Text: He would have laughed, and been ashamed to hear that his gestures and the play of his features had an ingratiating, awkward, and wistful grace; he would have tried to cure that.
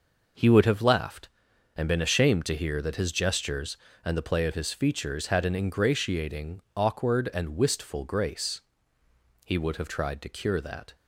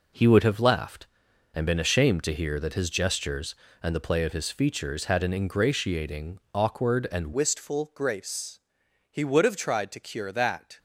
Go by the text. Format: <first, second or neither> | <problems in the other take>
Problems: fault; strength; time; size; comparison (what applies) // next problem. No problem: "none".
first | changes voice at "wistful"; from 7.3 s on; 3.4 s long